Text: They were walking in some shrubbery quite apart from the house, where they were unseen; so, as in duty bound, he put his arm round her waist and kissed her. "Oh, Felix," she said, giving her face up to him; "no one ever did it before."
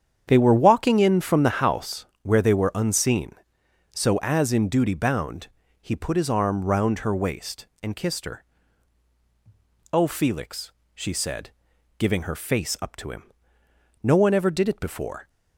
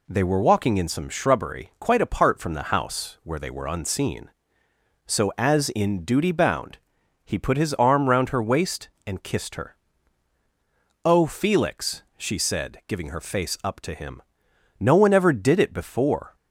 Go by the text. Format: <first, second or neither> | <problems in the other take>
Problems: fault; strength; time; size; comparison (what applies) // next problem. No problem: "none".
second | starts louder than the rest; strong; until 1.2 s; 8.5 dB // skips "some shrubbery quite apart"; at 1.2 s